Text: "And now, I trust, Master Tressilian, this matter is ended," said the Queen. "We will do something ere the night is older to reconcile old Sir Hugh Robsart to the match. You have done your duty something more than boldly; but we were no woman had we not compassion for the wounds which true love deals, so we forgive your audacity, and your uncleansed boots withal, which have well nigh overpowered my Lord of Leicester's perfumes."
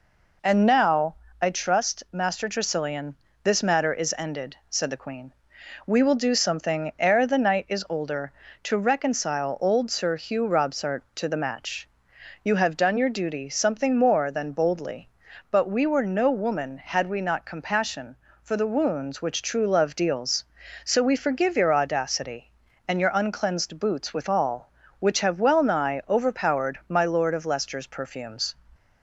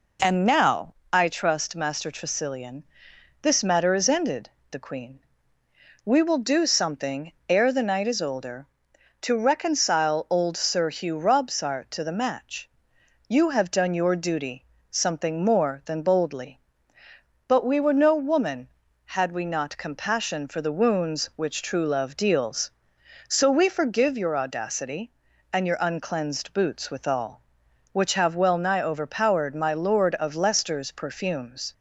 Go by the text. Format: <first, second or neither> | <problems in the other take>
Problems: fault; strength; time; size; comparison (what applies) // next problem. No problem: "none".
first | skips "said"; at 4.6 s // pauses between "something" and "ere"; slight; at 7.3 s; 0.16 s long // pauses between "duty" and "something"; slight; at 14.6 s; 0.28 s long